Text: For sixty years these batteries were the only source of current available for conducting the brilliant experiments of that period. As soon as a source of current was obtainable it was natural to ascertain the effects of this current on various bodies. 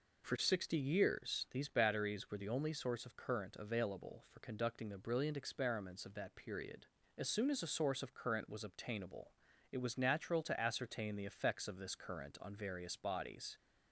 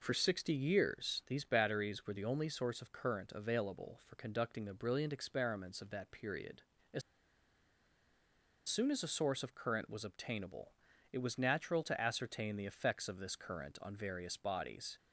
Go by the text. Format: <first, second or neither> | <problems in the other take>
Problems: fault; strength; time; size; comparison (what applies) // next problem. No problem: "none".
first | pauses between "As" and "soon"; strong; at 7.0 s; 1.6 s long // pauses between "obtainable" and "it"; at 10.7 s; 0.40 s long; also in the first